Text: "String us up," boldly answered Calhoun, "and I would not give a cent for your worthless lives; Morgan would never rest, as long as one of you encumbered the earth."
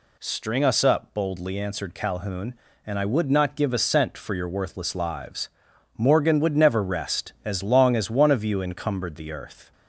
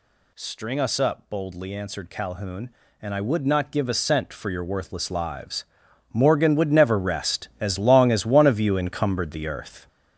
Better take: first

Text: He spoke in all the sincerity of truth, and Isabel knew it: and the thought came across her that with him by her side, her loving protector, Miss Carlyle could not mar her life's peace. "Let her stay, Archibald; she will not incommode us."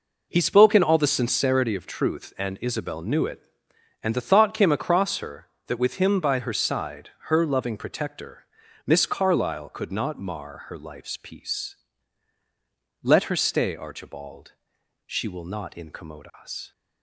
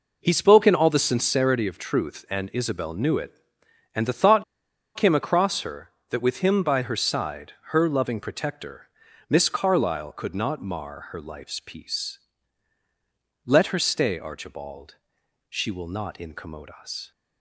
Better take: first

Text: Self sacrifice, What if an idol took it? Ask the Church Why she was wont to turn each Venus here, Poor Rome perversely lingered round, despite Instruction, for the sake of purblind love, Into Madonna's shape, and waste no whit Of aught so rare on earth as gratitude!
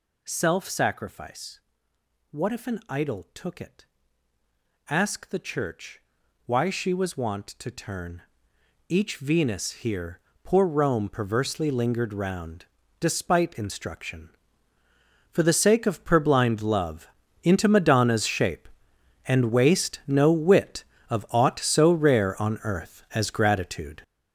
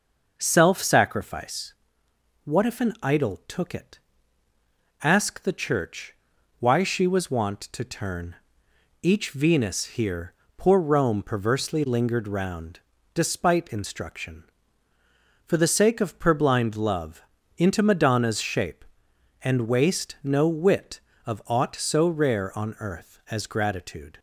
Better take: second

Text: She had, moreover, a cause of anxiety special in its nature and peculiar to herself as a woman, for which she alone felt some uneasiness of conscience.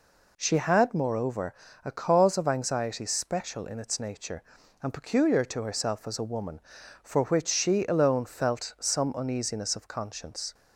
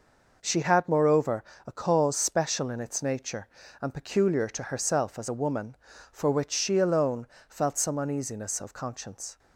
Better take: first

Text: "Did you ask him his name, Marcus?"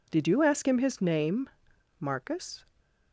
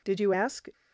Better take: first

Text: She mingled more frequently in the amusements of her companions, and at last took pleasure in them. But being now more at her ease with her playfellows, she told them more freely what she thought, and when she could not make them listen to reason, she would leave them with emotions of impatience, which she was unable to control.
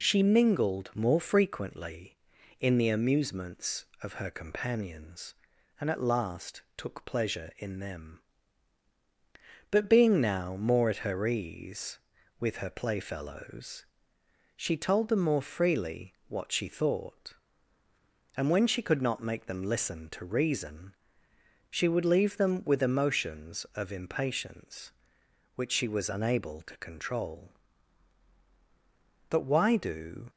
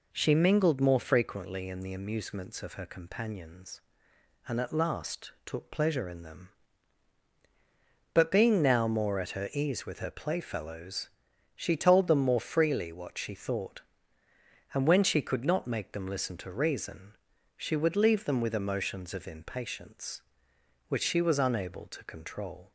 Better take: second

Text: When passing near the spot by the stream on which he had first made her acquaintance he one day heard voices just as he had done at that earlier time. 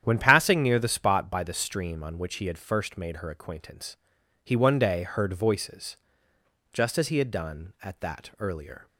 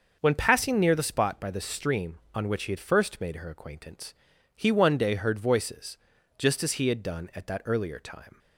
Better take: second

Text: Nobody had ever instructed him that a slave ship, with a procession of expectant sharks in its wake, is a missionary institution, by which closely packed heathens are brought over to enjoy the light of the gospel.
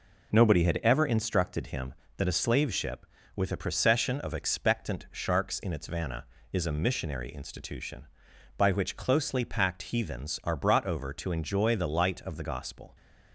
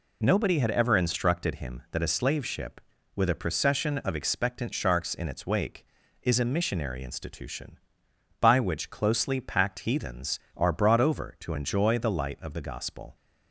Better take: second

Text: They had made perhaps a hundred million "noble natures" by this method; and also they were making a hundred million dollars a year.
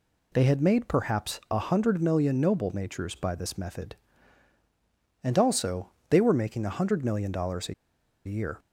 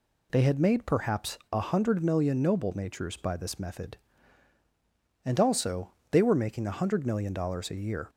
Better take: second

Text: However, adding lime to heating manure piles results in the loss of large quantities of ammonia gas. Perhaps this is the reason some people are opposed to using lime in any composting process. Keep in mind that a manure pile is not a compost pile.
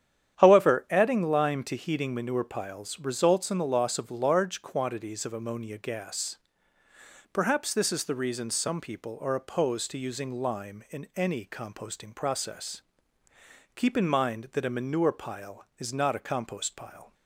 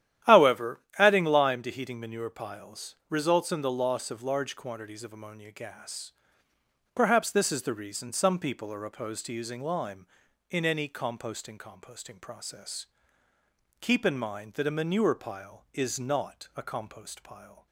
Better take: first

